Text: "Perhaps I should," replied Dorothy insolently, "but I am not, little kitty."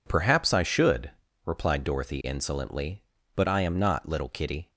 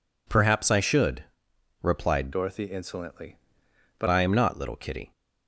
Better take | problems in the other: first | changes voice from "Dorothy" to "but"; from 2.3 to 4.0 s; 1.7 s long

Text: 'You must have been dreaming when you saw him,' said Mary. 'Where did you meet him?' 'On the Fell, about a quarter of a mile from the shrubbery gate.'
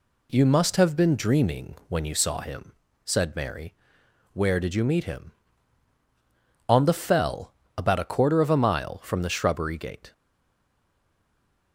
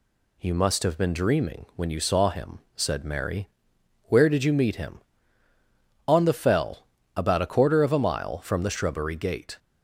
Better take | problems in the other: second | stays silent after the last word; noticeable; from 10.1 s on; 1.6 s long

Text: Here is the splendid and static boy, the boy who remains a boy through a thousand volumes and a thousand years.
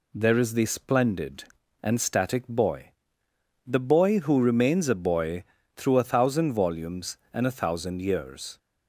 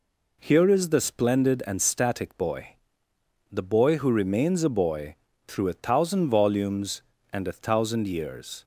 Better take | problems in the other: second | says "There" for "Here"; at 0.1 s // pauses between "boy" and "through"; slight; at 5.4 s; 0.34 s long; slight in the second

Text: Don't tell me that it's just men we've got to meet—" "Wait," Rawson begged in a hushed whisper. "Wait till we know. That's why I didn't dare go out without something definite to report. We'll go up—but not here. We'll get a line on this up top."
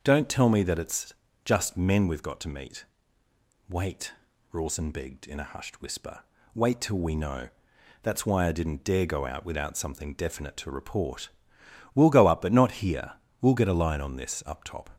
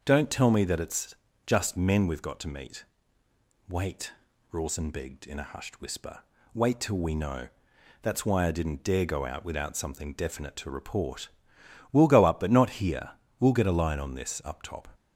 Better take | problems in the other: neither | starts louder than the rest; the same in both // pauses between "it's" and "just"; slight; the same in both

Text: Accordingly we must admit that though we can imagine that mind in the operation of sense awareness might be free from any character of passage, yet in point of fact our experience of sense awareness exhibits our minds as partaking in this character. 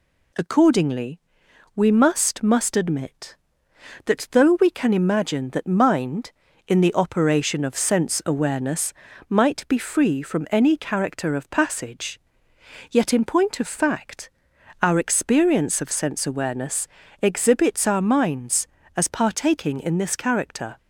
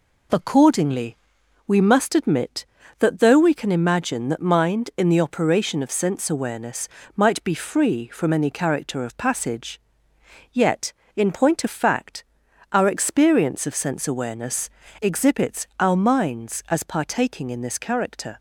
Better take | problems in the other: second | pauses between "Accordingly" and "we"; noticeable; at 1.1 s; 0.56 s long; noticeable in the second // says "must" twice; at 2.4 s // pauses between "awareness" and "might"; slight; at 8.9 s; 0.36 s long; slight in the second // pauses between "fact" and "our"; noticeable; at 14.3 s; 0.50 s long; noticeable in the second // pauses between "awareness" and "exhibits"; slight; at 16.8 s; 0.34 s long; slight in the second

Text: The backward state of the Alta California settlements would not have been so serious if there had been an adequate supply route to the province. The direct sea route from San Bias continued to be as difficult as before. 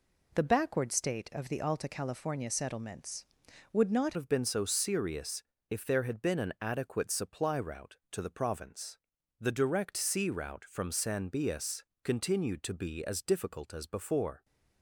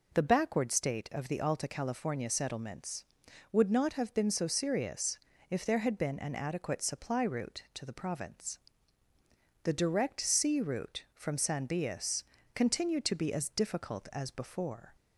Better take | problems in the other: second | changes voice at "have"; from 4.1 s on; 10.3 s long // pauses between "serious" and "if"; slight; at 5.4 s; 0.26 s long; slight in the second // pauses between "Bias" and "continued"; slight; at 11.8 s; 0.22 s long; slight in the second

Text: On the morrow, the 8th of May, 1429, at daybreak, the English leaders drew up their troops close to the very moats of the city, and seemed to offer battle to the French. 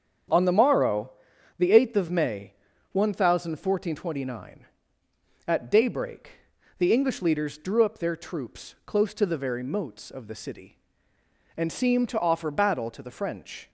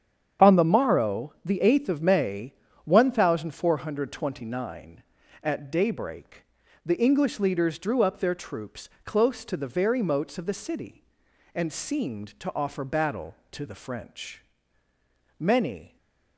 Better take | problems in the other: first | starts louder than the rest; strong; until 1.5 s; 8.5 dB; strong in the first // pauses between "troops" and "close"; slight; at 8.8 s; 0.16 s long // goes on to say "Many"; from 15.3 s on; 0.58 s long // stays silent after the last word; slight; from 15.8 s on; 0.5 s long

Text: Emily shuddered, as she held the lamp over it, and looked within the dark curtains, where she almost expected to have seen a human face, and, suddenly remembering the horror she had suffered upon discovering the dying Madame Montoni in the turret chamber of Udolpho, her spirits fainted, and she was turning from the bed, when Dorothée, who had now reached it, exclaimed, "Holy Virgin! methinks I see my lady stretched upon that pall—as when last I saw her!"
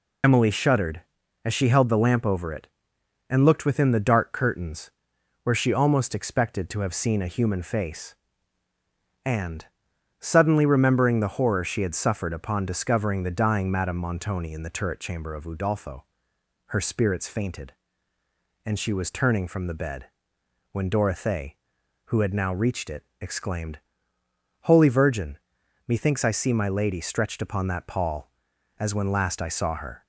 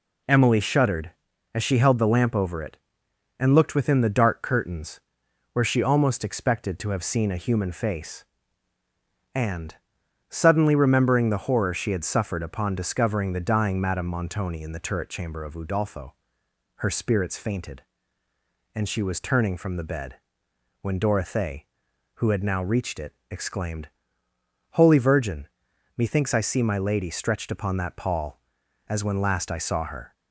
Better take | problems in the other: second | loses the start of "Emily"; at 0.2 s; 85 ms

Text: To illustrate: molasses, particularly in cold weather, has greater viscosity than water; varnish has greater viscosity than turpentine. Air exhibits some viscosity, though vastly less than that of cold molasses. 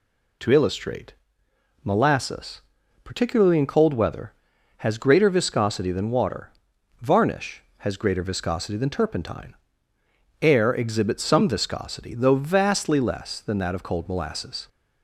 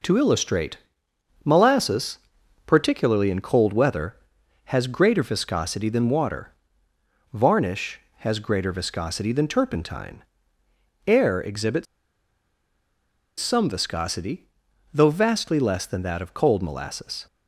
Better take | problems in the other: first | pauses between "exhibits" and "some"; strong; at 11.8 s; 1.5 s long

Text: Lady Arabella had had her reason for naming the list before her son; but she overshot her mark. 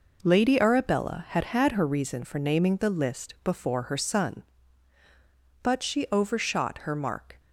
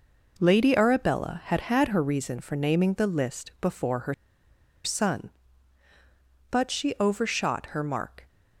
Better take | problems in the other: first | pauses between "her" and "son"; noticeable; at 4.1 s; 0.71 s long

